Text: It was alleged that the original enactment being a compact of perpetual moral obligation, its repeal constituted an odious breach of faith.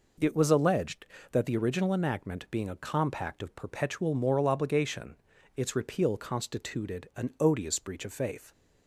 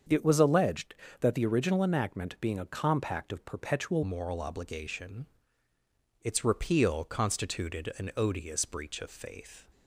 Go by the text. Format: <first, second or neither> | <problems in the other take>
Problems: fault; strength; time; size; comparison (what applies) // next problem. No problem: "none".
first | starts louder than the rest; until 1.3 s; 7 dB // changes voice at "moral"; from 4.0 s on; 5.6 s long